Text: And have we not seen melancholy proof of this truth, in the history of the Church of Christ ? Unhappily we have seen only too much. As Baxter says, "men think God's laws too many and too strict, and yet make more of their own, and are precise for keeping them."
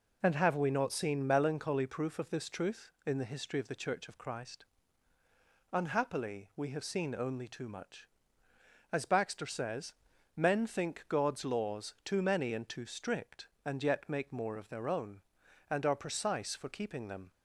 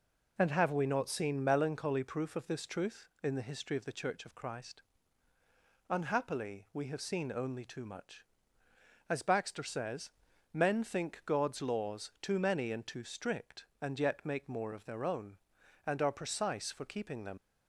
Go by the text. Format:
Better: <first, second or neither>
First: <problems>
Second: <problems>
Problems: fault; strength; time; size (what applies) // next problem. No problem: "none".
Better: first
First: none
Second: leaves "them" unfinished; at 17.3 s; 85 ms